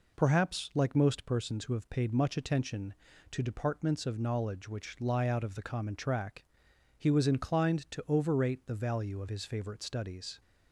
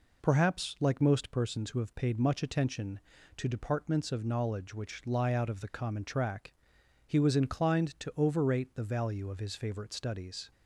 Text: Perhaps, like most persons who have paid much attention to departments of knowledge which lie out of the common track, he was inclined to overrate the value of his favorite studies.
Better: neither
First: none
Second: none

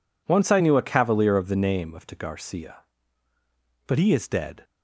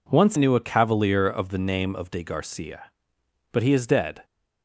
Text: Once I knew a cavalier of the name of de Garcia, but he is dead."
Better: first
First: none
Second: skips "I"; at 0.3 s

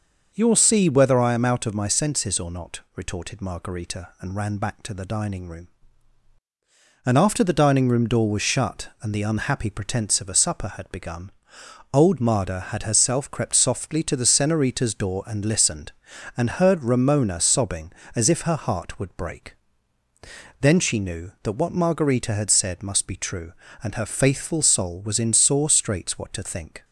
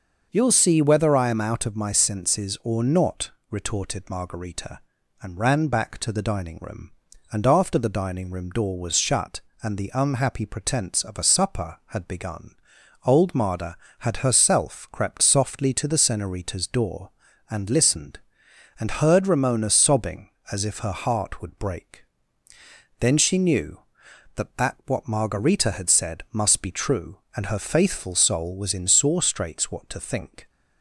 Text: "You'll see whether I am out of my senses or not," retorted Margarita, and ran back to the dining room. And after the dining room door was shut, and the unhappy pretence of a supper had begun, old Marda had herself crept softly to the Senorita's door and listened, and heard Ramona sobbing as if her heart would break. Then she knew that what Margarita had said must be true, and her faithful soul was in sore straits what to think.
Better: first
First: none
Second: starts louder than the rest; noticeable; until 1.3 s; 6 dB // says "that" twice; at 24.5 s

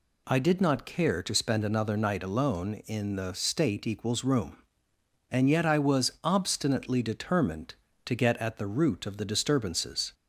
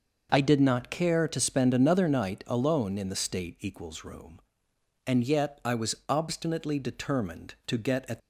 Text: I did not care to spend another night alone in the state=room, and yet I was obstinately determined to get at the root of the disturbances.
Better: first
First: none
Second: stops before "the root of the disturbances"; at 8.2 s

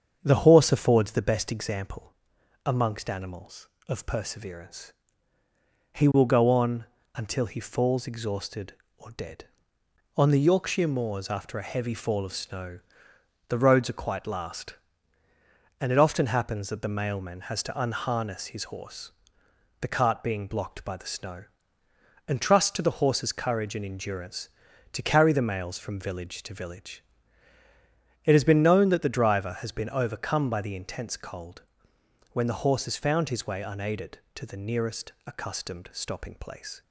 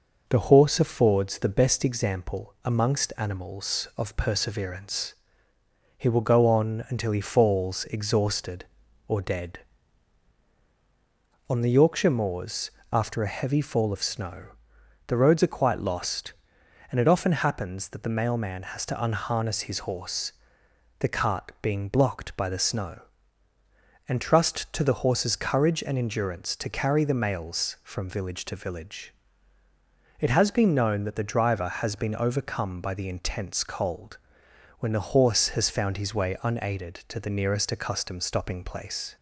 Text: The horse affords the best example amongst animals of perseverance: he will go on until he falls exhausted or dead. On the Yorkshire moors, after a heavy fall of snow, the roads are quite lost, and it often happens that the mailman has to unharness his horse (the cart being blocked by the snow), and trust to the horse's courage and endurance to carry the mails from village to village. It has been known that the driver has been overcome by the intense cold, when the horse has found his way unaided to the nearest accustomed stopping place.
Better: second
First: starts louder than the rest; strong; until 1.2 s; 7.5 dB // pauses between "example" and "amongst"; noticeable; at 2.1 s; 0.54 s long // pauses between "on" and "until"; slight; at 6.8 s; 0.30 s long // says "last" for "lost"; at 14.2 s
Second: none

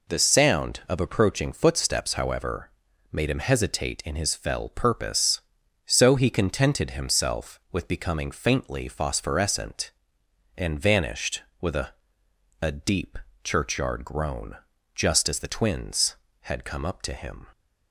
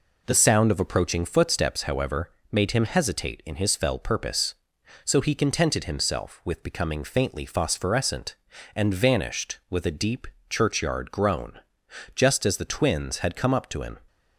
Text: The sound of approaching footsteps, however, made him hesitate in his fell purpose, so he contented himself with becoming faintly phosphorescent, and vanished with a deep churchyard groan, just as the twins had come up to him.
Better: second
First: says "a" twice; at 12.6 s // pauses between "deep" and "churchyard"; slight; at 13.1 s; 0.26 s long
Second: pauses between "deep" and "churchyard"; slight; at 10.2 s; 0.22 s long

